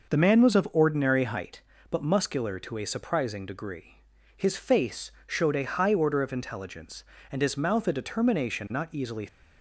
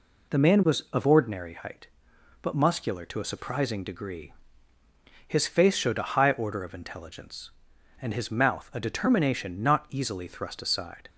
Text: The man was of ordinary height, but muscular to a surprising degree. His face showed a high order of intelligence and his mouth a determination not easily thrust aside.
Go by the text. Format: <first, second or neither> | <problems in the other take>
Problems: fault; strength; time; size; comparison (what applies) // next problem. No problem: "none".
second | pauses between "face" and "showed"; slight; at 5.0 s; 0.16 s long // stops before "thrust aside"; at 9.2 s